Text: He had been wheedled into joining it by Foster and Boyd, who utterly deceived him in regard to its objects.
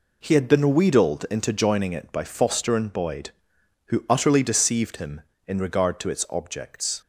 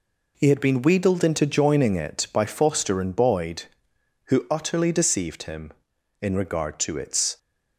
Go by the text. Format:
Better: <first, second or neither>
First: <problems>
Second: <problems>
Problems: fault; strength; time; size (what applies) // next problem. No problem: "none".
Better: first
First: none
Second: stops before "objects"; at 7.3 s